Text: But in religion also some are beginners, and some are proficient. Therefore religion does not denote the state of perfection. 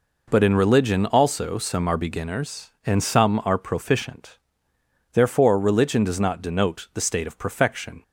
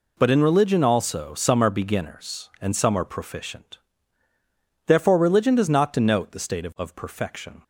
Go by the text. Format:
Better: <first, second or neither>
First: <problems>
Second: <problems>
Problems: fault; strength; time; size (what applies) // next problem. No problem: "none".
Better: first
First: none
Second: says "of" twice; at 6.7 s